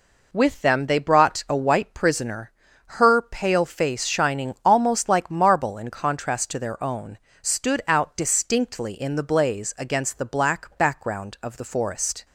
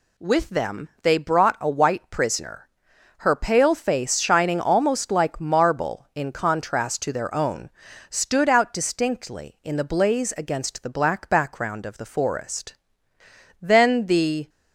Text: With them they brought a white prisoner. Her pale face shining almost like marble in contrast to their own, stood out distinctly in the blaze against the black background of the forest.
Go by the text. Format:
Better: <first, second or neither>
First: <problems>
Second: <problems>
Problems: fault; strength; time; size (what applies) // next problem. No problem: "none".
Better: first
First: none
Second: goes on to say "Then the"; noticeable; from 13.6 s on; 0.88 s long